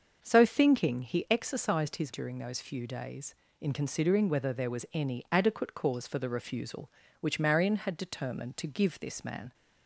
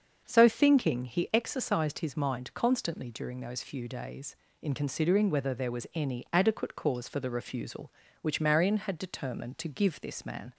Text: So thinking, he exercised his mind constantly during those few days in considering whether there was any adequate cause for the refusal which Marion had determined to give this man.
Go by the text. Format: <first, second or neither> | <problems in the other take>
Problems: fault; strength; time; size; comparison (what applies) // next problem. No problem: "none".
second | starts louder than the rest; until 1.2 s; 6.5 dB; also in the second // skips "mind constantly"; at 2.1 s